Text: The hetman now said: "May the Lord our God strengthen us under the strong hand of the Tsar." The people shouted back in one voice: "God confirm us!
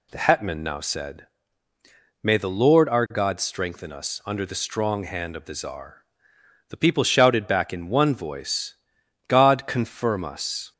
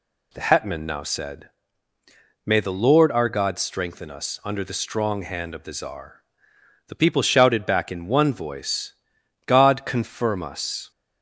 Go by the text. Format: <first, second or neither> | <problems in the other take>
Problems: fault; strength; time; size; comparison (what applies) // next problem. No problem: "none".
neither | none